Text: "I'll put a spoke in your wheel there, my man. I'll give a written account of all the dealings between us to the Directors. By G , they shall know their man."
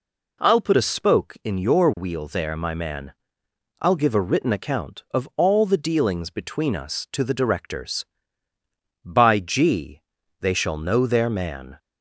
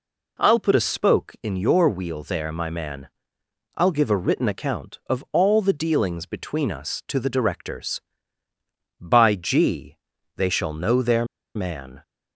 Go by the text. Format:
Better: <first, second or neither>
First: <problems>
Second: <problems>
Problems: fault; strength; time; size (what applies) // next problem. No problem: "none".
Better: first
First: none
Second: pauses between "their" and "man"; slight; at 11.2 s; 0.29 s long